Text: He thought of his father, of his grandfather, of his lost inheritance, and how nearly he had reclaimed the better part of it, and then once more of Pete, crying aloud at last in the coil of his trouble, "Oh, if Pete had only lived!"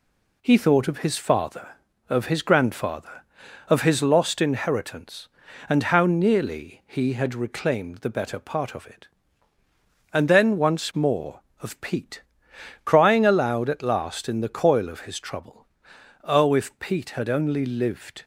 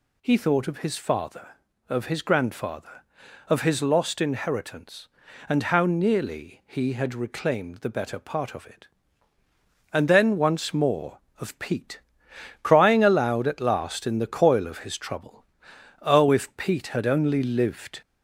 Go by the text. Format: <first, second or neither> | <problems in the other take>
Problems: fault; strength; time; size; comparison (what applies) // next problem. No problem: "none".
first | gets louder; slight; throughout; 2 dB